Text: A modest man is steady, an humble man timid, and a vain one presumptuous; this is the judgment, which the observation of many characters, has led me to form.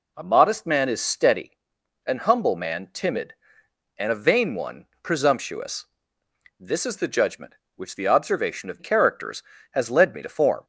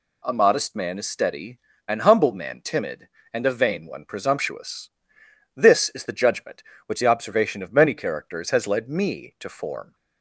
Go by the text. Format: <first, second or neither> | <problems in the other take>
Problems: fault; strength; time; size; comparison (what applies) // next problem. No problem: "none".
second | pauses between "one" and "presumptuous"; slight; at 4.8 s; 0.16 s long // skips "many"; at 8.7 s